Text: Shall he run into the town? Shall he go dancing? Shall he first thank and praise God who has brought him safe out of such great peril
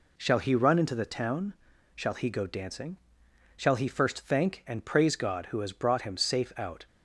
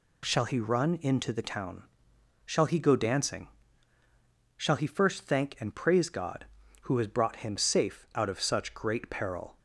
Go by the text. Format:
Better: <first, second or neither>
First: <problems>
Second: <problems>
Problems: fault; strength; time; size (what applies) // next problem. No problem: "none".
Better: second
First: stops before "of such great peril"; at 6.8 s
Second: none